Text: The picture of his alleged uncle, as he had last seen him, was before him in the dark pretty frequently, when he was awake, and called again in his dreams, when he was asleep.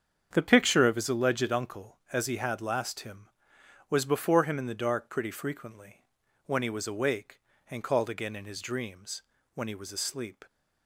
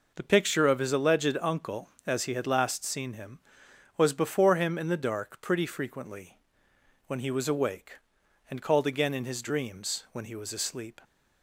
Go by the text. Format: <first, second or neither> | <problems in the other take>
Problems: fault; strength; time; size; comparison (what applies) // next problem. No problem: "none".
second | starts louder than the rest; strong; until 1.3 s; 7.5 dB // skips "seen"; at 2.9 s